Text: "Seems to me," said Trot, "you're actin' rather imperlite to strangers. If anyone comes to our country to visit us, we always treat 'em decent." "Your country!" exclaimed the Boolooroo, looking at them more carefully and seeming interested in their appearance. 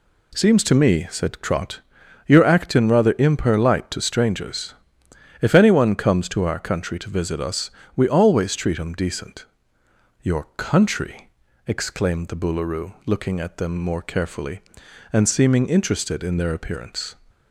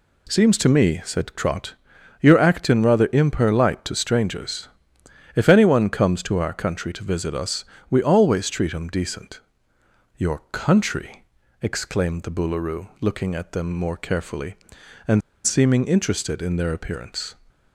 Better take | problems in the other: first | pauses between "and" and "seeming"; slight; at 15.2 s; 0.26 s long

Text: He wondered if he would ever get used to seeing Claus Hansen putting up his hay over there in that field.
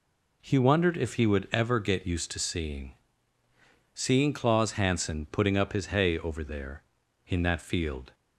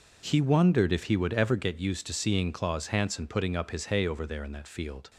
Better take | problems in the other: second | says "seeing" twice; at 3.9 s

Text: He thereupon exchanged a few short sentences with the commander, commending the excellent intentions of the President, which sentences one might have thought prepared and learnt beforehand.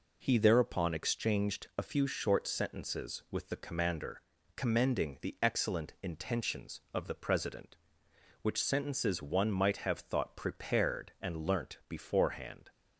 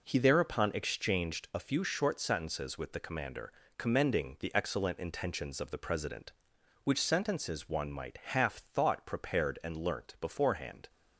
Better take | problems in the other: first | says "half" for "have"; at 8.1 s

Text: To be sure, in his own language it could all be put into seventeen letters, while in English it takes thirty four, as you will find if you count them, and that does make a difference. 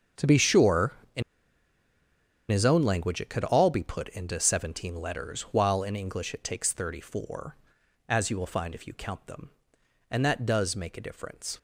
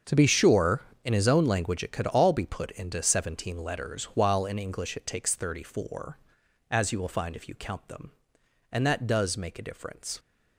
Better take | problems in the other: second | starts louder than the rest; until 2.6 s; 7 dB; also in the second // pauses between "in" and "his"; strong; at 1.2 s; 1.2 s long

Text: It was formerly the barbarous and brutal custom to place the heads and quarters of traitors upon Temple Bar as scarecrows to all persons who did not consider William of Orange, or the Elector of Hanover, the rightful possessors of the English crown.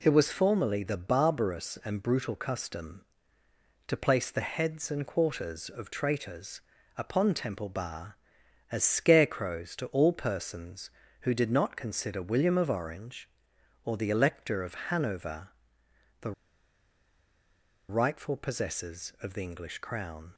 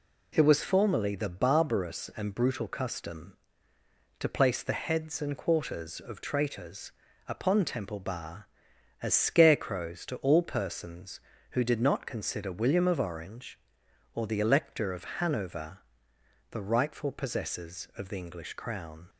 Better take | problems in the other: second | pauses between "traitors" and "upon"; at 6.5 s; 0.38 s long; also in the second // pauses between "of" and "Hanover"; slight; at 14.7 s; 0.16 s long; slight in the second // pauses between "the" and "rightful"; strong; at 16.3 s; 1.5 s long

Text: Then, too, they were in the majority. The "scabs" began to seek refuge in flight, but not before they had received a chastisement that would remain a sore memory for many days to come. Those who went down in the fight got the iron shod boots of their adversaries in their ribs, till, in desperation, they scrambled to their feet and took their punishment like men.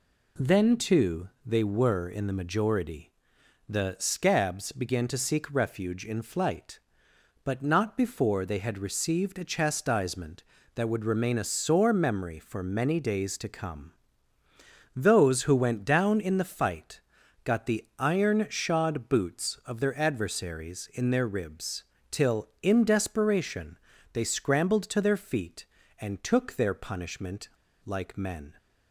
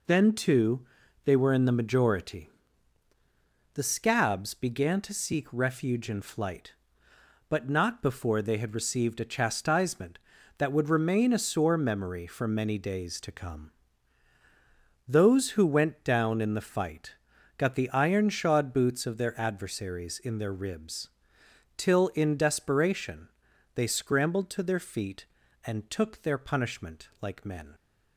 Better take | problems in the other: second | pauses between "fight" and "got"; at 17.0 s; 0.42 s long; also in the second // pauses between "punishment" and "like"; slight; at 27.4 s; 0.34 s long

